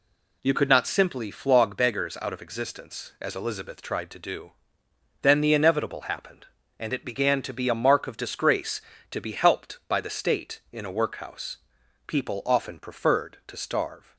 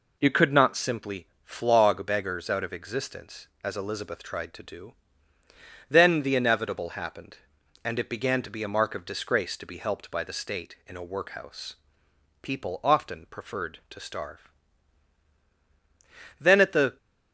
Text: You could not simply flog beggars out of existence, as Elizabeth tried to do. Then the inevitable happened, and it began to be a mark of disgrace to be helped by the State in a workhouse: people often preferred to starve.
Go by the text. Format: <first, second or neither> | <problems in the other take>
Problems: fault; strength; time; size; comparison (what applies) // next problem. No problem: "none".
first | pauses between "simply" and "flog"; slight; at 1.2 s; 0.18 s long // goes on to say "Then at the"; from 16.4 s on; 0.56 s long